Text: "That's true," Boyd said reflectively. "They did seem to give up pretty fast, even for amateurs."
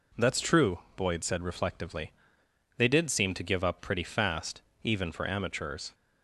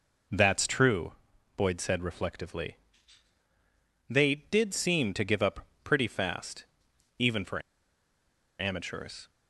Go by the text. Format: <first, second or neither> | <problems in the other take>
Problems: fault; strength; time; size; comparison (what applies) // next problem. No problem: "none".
first | pauses between "up" and "pretty"; slight; at 5.6 s; 0.16 s long // pauses between "for" and "amateurs"; noticeable; at 7.6 s; 0.97 s long